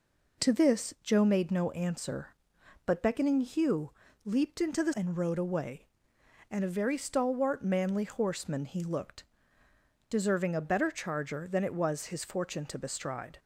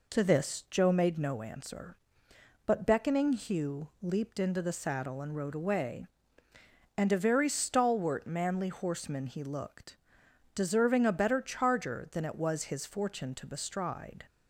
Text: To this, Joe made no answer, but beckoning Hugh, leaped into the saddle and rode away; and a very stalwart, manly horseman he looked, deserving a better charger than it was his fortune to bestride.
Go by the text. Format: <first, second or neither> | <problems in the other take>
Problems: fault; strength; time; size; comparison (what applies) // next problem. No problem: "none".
second | skips "saddle"; at 4.9 s